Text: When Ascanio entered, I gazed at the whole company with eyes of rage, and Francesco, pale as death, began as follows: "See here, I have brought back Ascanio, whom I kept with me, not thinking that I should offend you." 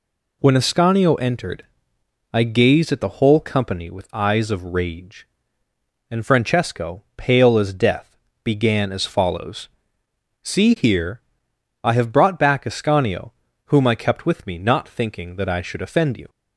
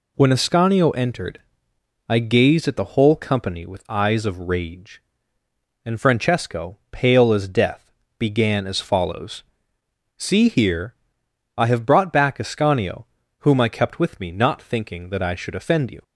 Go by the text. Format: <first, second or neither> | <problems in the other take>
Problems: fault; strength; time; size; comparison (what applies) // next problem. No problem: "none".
neither | none